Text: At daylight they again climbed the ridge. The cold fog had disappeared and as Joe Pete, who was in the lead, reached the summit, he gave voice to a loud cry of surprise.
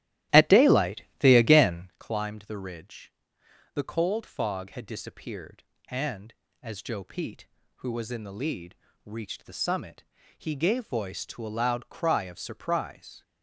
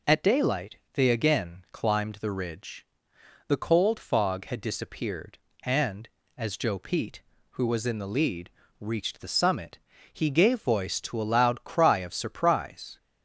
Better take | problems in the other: second | starts louder than the rest; strong; until 2.0 s; 13.5 dB // pauses between "daylight" and "they"; slight; at 1.0 s; 0.18 s long; slight in the second

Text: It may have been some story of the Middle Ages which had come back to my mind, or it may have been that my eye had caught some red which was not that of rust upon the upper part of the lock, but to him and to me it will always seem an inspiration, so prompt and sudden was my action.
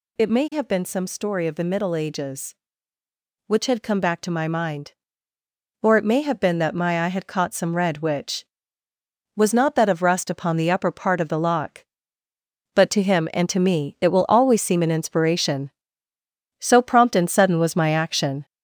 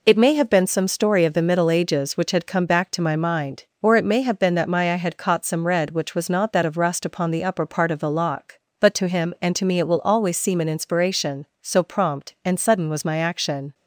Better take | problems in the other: second | gets louder; noticeable; throughout; 5 dB

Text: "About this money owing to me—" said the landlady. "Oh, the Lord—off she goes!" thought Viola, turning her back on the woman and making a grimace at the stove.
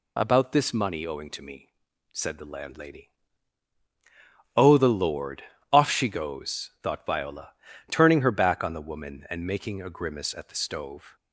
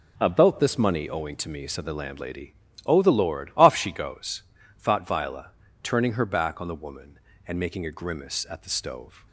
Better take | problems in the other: neither | none

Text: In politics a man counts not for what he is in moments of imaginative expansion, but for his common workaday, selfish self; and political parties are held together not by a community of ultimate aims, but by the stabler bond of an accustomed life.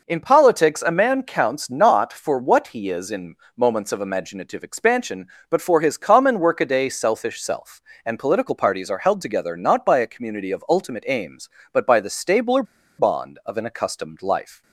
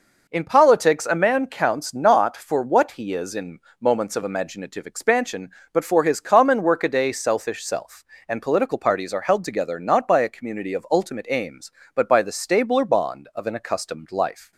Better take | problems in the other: second | pauses between "in" and "moments"; slight; at 3.3 s; 0.20 s long; slight in the second // pauses between "stabler" and "bond"; slight; at 12.6 s; 0.35 s long

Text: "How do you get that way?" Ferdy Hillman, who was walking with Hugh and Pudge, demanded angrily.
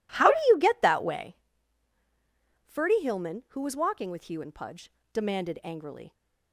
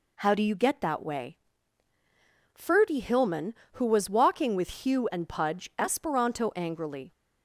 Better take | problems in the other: first | says "esperanto" for "demanded"; at 5.7 s

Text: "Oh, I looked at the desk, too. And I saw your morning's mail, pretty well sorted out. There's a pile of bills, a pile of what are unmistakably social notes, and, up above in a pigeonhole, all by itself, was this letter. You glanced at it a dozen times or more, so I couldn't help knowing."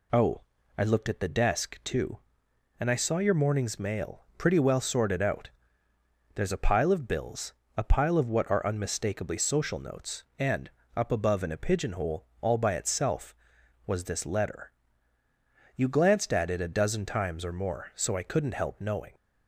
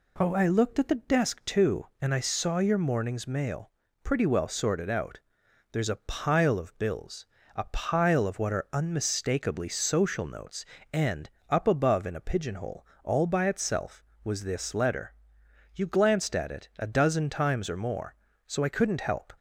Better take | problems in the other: first | stops before "knowing"; at 19.3 s

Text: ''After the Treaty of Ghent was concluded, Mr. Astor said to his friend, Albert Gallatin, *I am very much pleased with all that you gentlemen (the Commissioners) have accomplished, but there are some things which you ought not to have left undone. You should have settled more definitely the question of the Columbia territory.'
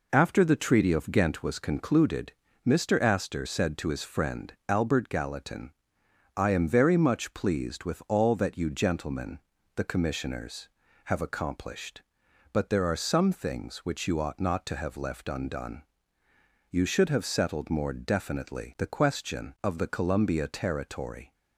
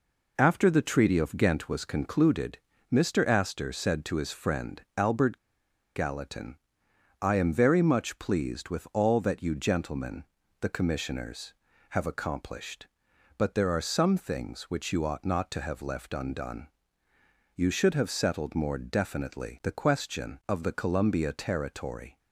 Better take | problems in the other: first | pauses between "Albert" and "Gallatin"; noticeable; at 5.3 s; 0.57 s long

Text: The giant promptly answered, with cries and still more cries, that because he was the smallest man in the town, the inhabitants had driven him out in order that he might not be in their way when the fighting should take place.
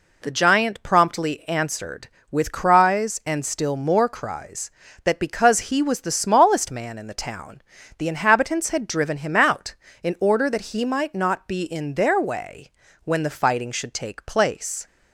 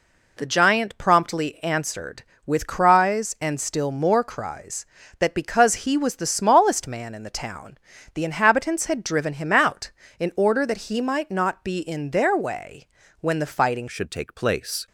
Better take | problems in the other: first | pauses between "way" and "when"; slight; at 12.8 s; 0.34 s long; slight in the first // changes voice at "should"; from 13.8 s on; 1.0 s long

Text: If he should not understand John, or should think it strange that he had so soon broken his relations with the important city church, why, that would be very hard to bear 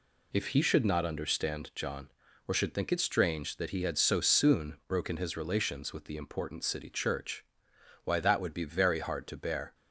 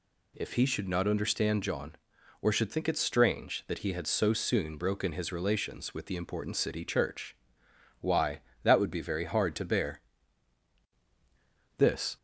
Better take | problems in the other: first | goes on to say "This"; slight; from 11.7 s on; 0.40 s long

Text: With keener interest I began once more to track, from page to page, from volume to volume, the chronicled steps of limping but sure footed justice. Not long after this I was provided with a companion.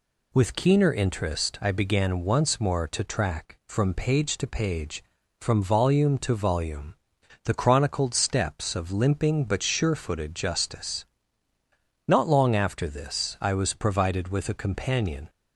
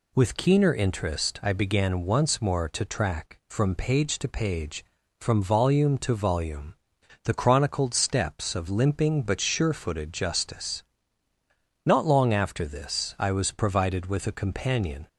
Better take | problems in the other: neither | none

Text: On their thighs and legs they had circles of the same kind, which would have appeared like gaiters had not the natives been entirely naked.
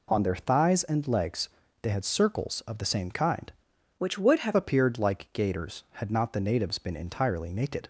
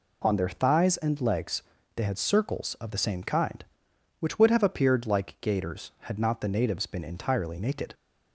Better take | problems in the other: second | pauses between "legs" and "they"; slight; at 1.4 s; 0.34 s long; slight in the second // changes voice from "which" to "have"; from 3.9 to 4.5 s; 0.6 s long

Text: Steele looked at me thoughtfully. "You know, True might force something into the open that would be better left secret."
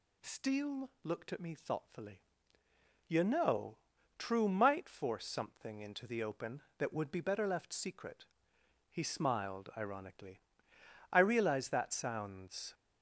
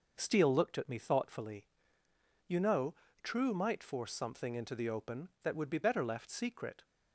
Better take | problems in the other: second | goes on to say "He smiled ironically I realize that sounds"; strong; from 8.9 s on; 3.8 s long

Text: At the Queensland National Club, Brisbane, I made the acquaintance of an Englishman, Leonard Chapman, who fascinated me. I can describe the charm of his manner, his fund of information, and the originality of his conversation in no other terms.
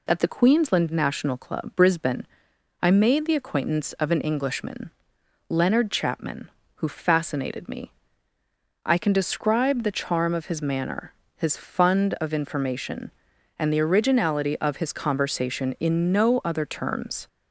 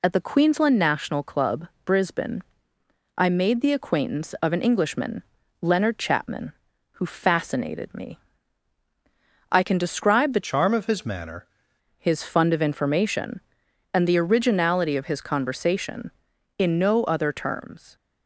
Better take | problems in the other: first | changes voice from "charm" to "manner"; from 10.4 to 11.4 s; 1.0 s long

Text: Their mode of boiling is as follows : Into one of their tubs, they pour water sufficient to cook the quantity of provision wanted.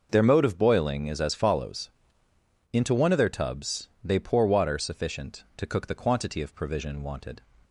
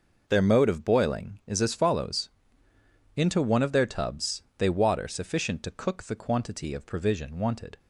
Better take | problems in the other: first | skips "pour"; at 4.6 s

